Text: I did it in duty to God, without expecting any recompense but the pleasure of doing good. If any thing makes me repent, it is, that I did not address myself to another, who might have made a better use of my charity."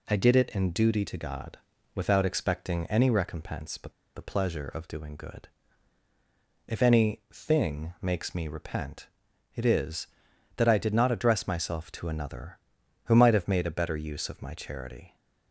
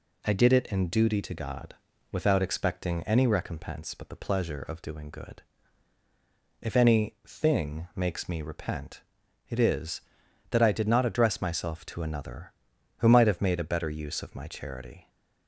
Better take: second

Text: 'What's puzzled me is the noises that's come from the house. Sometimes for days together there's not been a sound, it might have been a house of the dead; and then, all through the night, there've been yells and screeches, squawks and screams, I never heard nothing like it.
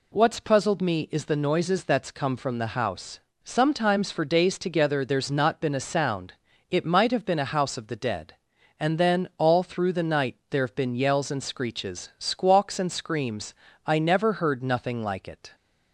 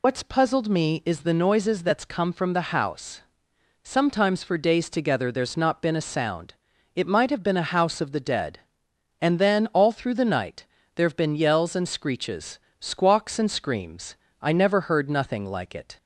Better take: first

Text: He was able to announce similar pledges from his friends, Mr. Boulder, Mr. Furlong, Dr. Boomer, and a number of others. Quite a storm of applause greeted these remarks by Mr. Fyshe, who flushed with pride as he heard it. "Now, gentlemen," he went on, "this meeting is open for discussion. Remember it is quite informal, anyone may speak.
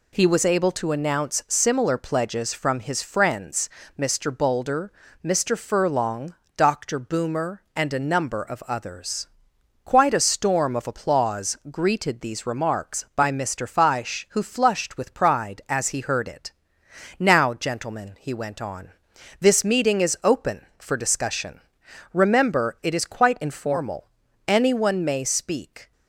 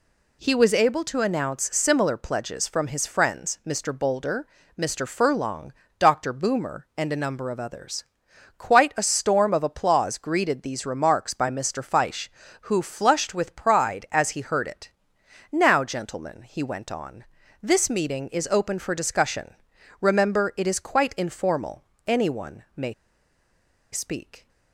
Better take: first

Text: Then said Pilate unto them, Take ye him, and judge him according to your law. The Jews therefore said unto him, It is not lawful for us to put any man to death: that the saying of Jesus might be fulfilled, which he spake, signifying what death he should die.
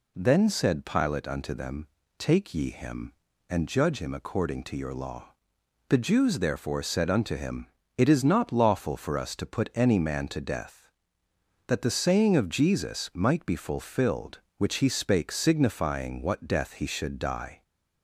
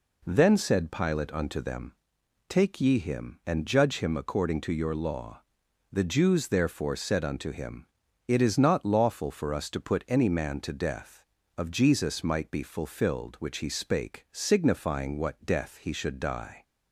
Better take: first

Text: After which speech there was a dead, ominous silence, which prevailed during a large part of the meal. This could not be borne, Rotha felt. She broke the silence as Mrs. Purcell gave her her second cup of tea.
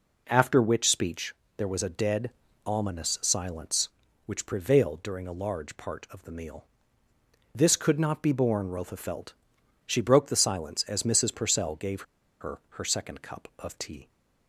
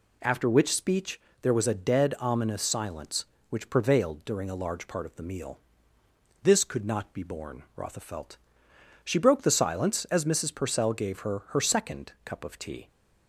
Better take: second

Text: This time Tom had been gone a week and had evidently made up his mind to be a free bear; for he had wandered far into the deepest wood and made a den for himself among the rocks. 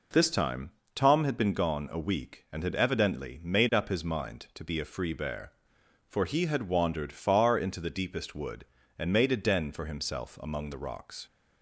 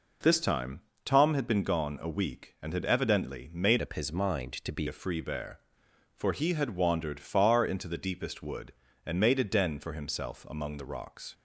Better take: first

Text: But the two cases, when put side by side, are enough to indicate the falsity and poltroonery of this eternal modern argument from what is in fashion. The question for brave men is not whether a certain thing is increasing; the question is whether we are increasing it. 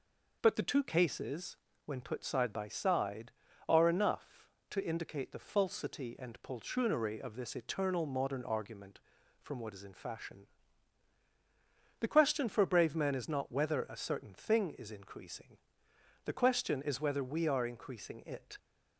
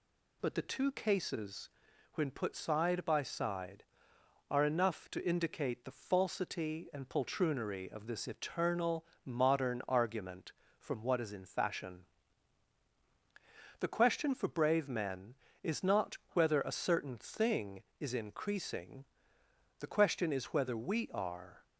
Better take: first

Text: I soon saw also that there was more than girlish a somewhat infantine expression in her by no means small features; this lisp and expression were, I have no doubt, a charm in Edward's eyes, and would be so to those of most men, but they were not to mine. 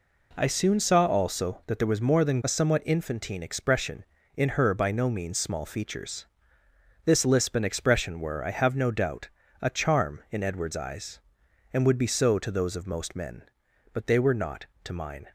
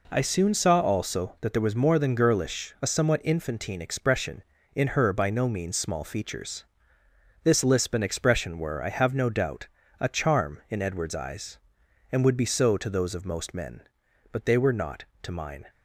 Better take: second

